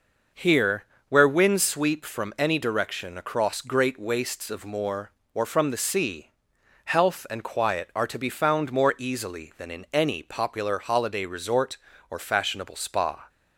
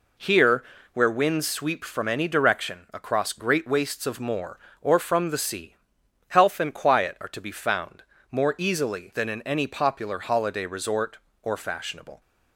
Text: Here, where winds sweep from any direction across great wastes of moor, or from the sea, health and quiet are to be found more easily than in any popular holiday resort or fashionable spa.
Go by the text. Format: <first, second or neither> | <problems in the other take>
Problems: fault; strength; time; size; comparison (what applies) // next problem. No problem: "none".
first | pauses between "found" and "more"; slight; at 8.0 s; 0.30 s long // stops before "spa"; at 12.2 s